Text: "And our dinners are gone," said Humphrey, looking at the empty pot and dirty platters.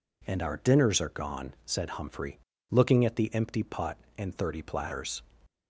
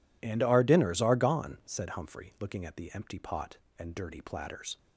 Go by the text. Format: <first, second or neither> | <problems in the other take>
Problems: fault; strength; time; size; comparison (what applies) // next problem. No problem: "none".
second | says "thirty" for "dirty"; at 4.3 s